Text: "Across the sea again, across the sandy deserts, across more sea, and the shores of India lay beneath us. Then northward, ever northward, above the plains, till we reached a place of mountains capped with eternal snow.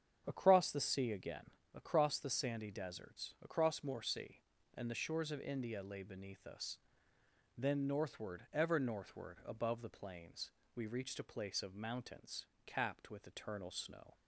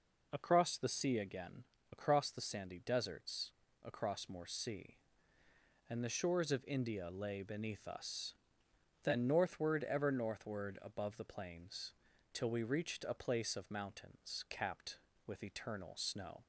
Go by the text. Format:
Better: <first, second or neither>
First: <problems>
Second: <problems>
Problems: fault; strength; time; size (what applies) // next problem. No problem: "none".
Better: second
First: starts louder than the rest; strong; until 1.2 s; 8 dB // skips "till"; at 10.6 s // pauses between "mountains" and "capped"; slight; at 12.4 s; 0.18 s long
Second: none